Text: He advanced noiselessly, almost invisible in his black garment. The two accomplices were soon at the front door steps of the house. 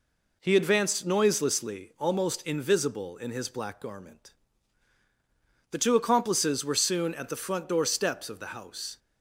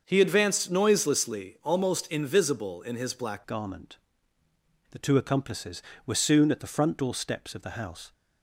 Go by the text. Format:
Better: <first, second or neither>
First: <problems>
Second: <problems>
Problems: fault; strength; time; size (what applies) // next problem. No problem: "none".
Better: first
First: none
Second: starts louder than the rest; until 1.0 s; 6.5 dB // changes voice at "garment"; from 3.4 s on; 4.7 s long